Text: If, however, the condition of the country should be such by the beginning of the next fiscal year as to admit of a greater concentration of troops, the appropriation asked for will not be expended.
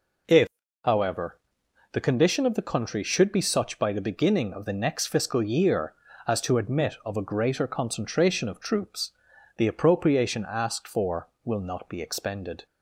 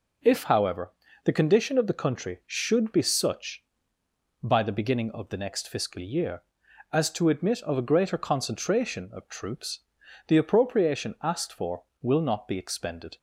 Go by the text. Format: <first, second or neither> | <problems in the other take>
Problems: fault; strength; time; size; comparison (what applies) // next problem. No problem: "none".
neither | none